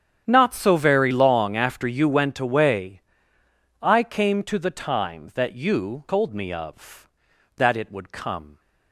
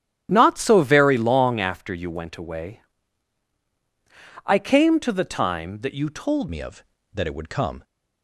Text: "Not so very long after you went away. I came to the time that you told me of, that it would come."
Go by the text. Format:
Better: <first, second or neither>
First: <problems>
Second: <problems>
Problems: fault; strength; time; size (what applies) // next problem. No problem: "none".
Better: first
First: starts louder than the rest; strong; until 1.2 s; 9 dB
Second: starts louder than the rest; strong; until 1.3 s; 11.5 dB // changes voice at "me"; from 6.4 s on; 1.4 s long